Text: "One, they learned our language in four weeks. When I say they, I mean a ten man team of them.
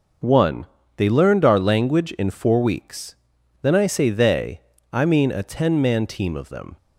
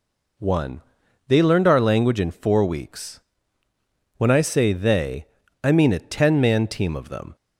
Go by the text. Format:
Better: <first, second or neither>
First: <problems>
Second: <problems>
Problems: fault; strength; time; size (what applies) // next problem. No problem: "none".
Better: second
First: says "Then" for "When"; at 3.6 s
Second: none